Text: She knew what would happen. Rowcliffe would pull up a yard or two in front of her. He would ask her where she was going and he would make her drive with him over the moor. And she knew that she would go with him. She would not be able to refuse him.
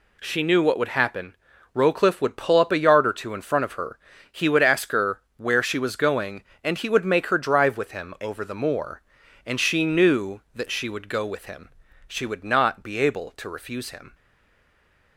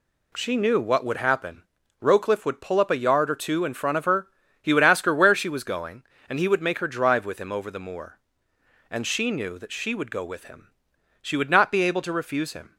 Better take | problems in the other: second | pauses between "her" and "where"; slight; at 5.1 s; 0.18 s long // stays silent after the last word; from 14.1 s on; 1.0 s long

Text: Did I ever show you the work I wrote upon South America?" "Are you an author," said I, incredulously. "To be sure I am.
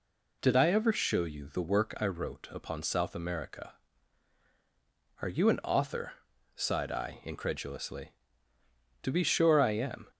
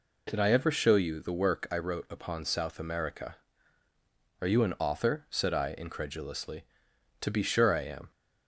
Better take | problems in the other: second | says "sighed" for "said"; at 6.5 s

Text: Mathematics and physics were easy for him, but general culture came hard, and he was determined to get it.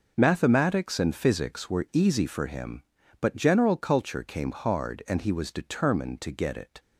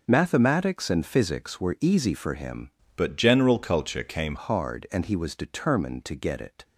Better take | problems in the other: first | changes voice from "but" to "came"; from 2.9 to 4.3 s; 1.4 s long

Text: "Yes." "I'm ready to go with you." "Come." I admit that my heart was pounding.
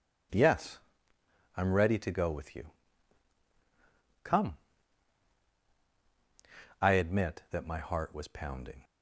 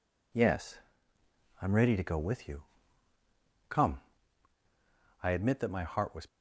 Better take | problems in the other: first | stops before "pounding"; at 6.2 s

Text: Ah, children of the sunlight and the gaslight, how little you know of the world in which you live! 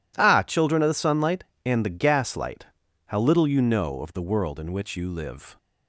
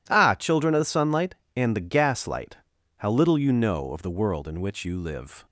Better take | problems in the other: neither | none

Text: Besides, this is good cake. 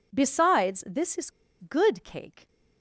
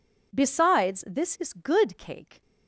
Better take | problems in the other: second | pauses between "is" and "good"; slight; at 1.2 s; 0.31 s long

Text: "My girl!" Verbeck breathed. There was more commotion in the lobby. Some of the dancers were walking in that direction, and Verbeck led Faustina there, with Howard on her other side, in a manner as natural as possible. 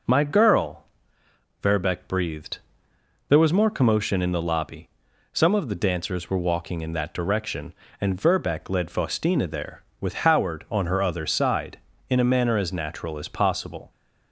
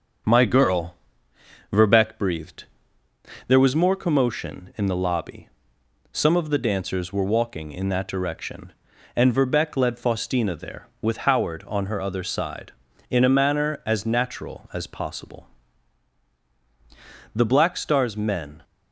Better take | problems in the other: first | starts louder than the rest; until 2.0 s; 7 dB // goes on to say "The Black Star's men"; noticeable; from 17.3 s on; 1.2 s long

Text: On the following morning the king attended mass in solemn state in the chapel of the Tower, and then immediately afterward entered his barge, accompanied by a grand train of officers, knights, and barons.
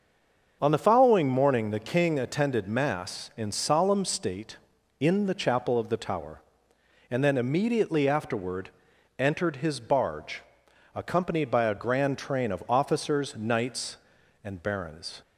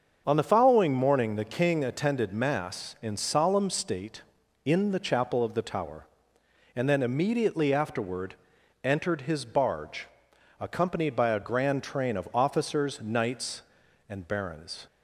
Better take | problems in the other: second | stays silent before the first word; slight; until 0.6 s; 0.6 s long // starts louder than the rest; until 1.6 s; 6.5 dB; also in the second // pauses between "afterward" and "entered"; noticeable; at 8.6 s; 0.48 s long; noticeable in the second

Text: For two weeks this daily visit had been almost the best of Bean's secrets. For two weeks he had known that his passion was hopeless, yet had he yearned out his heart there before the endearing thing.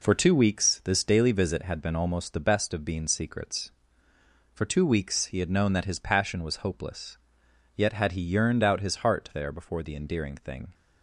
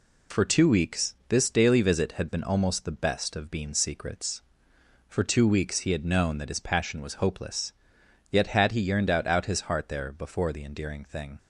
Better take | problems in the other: first | says "out" twice; at 9.2 s

